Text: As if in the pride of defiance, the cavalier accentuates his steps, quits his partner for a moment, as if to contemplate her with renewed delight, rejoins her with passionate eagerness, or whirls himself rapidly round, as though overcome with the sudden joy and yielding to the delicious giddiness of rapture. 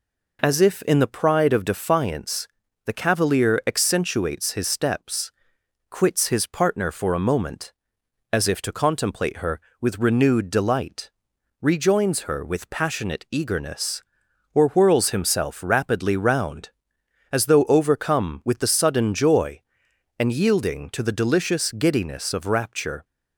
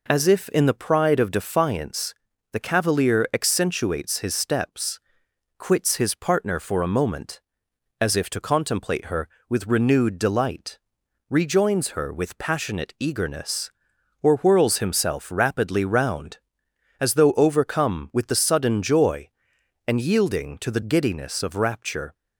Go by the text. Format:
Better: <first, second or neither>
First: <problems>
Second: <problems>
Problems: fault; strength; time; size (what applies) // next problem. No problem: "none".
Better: first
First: none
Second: skips "delicious"; at 20.8 s